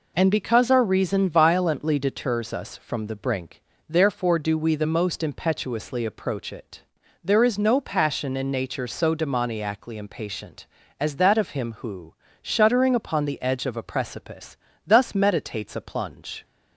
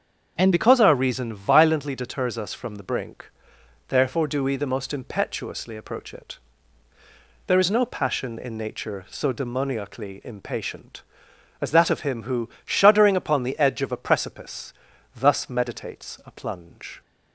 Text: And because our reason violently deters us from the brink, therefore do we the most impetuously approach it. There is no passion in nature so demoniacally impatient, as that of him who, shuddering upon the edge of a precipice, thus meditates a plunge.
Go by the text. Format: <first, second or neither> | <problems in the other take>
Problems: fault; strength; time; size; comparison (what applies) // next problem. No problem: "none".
first | starts louder than the rest; strong; until 1.3 s; 7.5 dB // changes voice at "because"; from 0.5 s on; 16.5 s long